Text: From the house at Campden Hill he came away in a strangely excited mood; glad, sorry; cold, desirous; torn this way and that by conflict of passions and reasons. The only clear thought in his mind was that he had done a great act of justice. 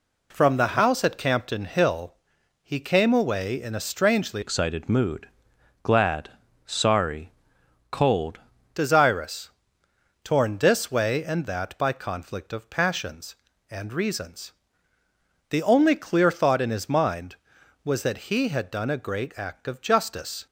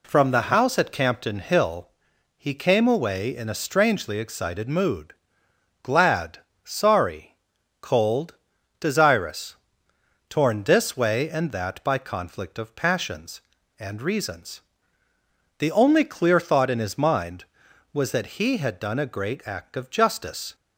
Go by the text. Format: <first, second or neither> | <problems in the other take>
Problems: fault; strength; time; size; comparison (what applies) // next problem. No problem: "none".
second | pauses between "Hill" and "he"; noticeable; at 2.1 s; 0.48 s long; noticeable in the second // changes voice from "excited" to "cold"; from 4.4 to 8.3 s; 3.9 s long